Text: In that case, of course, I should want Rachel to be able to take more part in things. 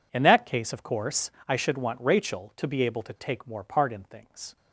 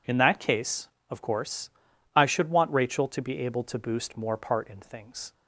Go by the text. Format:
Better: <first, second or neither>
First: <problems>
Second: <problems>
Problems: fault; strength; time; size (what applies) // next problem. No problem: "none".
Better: first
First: none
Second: says "boost" for "take"; at 3.7 s